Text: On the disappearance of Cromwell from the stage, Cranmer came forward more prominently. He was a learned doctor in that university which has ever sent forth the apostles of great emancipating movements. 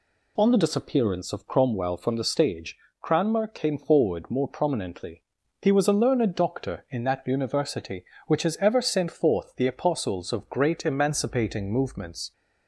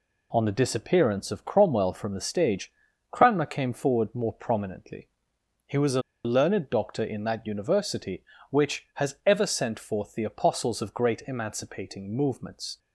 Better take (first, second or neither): first